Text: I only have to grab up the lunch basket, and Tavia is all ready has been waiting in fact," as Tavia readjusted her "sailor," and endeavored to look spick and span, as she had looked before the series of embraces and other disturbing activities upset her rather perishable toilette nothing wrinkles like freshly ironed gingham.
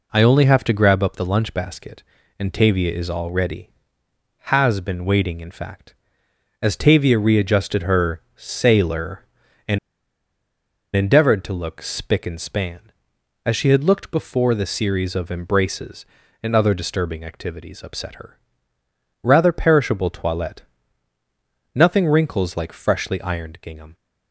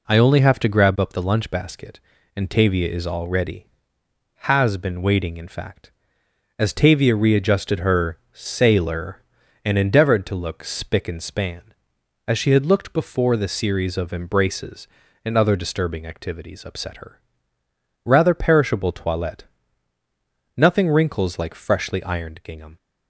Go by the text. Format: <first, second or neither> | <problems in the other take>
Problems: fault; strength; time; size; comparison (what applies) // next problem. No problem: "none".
second | pauses between "and" and "endeavored"; at 9.7 s; 1.1 s long // pauses between "her" and "rather"; noticeable; at 18.3 s; 0.86 s long; noticeable in the second // pauses between "toilette" and "nothing"; at 20.6 s; 1.1 s long; also in the second